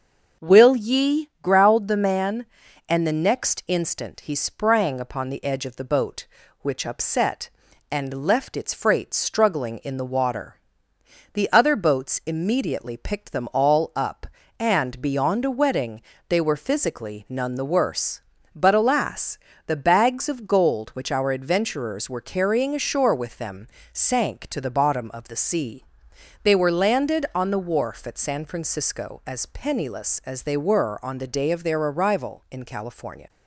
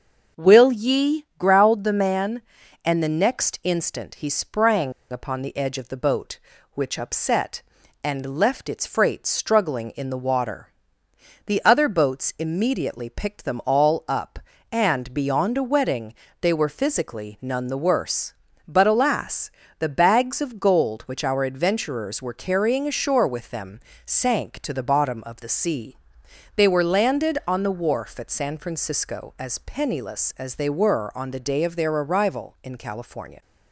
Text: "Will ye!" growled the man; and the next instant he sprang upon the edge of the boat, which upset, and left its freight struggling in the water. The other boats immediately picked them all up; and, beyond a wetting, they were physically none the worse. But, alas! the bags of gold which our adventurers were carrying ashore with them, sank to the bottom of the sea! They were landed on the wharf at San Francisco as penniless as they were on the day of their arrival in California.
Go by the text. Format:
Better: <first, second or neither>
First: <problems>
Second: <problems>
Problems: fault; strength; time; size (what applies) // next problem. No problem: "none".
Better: first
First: starts louder than the rest; until 1.5 s; 6.5 dB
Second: starts louder than the rest; until 1.4 s; 6.5 dB // pauses between "sprang" and "upon"; slight; at 4.9 s; 0.20 s long